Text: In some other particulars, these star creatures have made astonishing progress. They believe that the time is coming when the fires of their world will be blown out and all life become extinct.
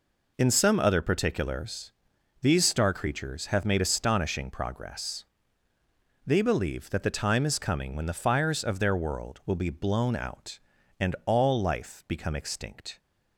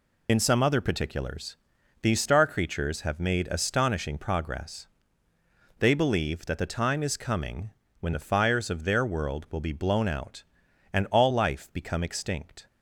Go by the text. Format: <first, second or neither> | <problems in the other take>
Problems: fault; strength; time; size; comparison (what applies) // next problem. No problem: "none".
first | loses the start of "In"; at 0.2 s; 70 ms // pauses between "coming" and "when"; slight; at 7.7 s; 0.28 s long